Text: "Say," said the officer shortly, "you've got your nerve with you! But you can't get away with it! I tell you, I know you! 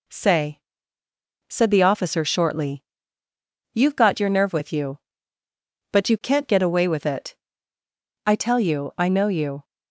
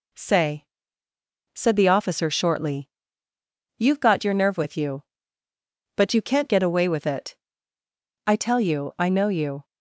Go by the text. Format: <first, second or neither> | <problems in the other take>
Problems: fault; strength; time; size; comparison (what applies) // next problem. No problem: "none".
neither | none